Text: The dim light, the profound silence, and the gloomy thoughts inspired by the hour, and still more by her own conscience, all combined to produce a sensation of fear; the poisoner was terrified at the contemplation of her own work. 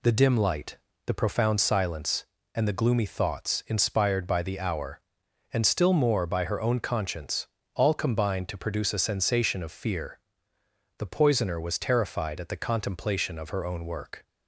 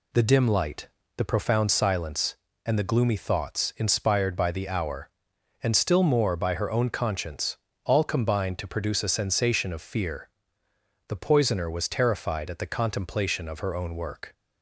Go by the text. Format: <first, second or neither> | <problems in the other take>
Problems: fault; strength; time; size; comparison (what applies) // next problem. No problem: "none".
neither | none